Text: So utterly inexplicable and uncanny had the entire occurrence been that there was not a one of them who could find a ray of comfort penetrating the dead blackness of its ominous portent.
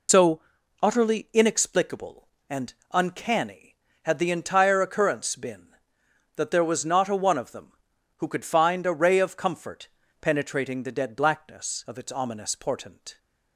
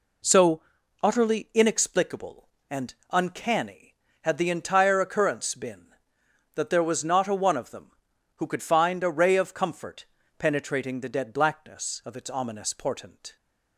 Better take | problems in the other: second | loses the start of "So"; at 0.0 s; 65 ms // pauses between "So" and "utterly"; at 0.4 s; 0.42 s long; also in the second // pauses between "and" and "uncanny"; slight; at 2.7 s; 0.18 s long; slight in the second // pauses between "comfort" and "penetrating"; slight; at 9.8 s; 0.34 s long; slight in the second

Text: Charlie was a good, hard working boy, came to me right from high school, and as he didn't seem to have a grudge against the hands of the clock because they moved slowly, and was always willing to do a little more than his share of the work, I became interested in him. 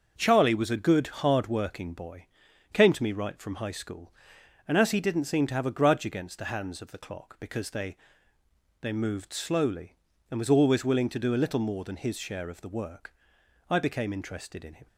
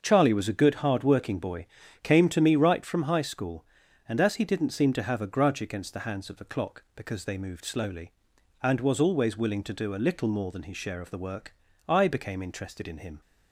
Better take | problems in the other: second | starts louder than the rest; until 1.1 s; 6.5 dB; also in the second // says "they" twice; at 8.8 s

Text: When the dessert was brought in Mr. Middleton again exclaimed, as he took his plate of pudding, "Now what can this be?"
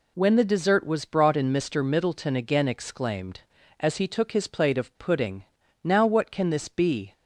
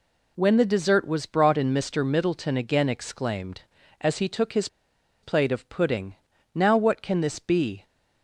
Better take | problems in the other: first | pauses between "his" and "plate"; noticeable; at 4.6 s; 0.55 s long

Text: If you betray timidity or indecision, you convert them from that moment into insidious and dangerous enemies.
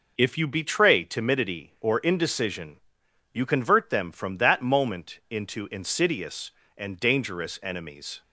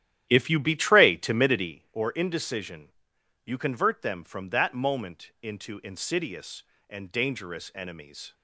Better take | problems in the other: first | starts louder than the rest; strong; until 1.8 s; 11.5 dB

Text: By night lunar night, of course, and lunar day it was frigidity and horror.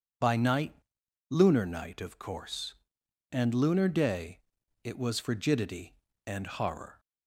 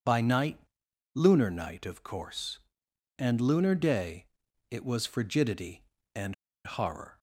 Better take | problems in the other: first | pauses between "night" and "lunar"; noticeable; at 0.5 s; 0.56 s long; noticeable in the first // pauses between "day" and "it"; at 4.2 s; 0.42 s long; also in the first // pauses between "and" and "horror"; slight; at 6.3 s; 0.30 s long

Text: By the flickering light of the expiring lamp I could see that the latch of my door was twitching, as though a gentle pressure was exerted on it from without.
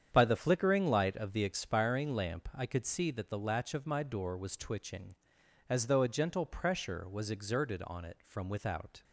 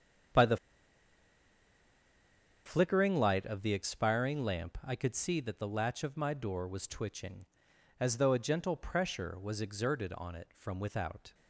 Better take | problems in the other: first | starts louder than the rest; strong; until 3.4 s; 8.5 dB; strong in the first // pauses between "the" and "flickering"; strong; at 0.5 s; 2.0 s long

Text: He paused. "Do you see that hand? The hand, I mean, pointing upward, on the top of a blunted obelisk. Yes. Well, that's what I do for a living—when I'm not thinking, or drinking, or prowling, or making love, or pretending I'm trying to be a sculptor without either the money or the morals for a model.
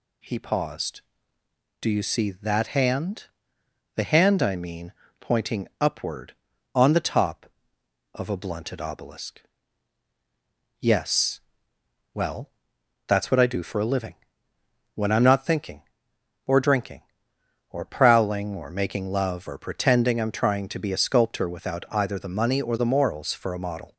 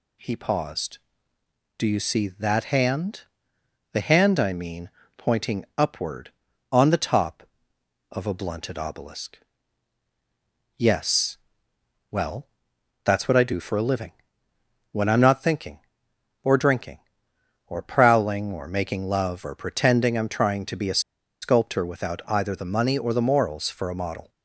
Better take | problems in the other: first | pauses between "a" and "sculptor"; at 20.9 s; 0.42 s long

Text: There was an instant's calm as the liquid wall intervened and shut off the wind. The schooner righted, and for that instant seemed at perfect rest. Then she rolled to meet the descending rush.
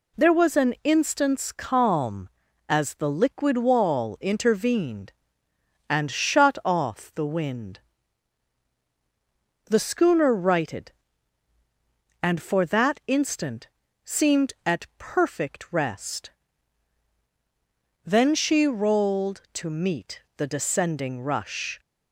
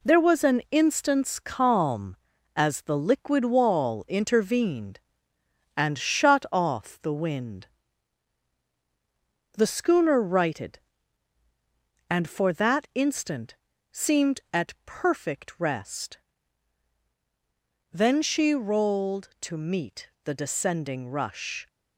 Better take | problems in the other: first | gets quieter; noticeable; throughout; 5 dB // pauses between "instant" and "seemed"; slight; at 13.5 s; 0.36 s long; slight in the first // pauses between "meet" and "the"; slight; at 20.0 s; 0.16 s long; slight in the first

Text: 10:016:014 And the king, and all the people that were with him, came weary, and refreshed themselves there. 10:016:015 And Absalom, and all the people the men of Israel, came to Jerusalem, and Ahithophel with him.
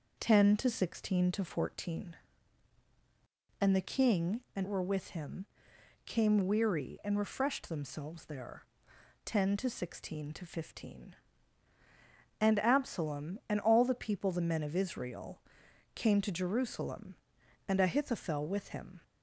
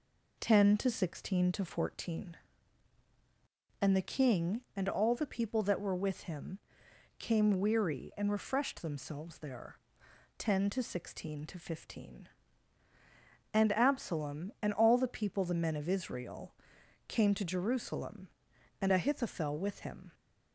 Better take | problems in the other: second | skips "all the people that"; at 4.6 s

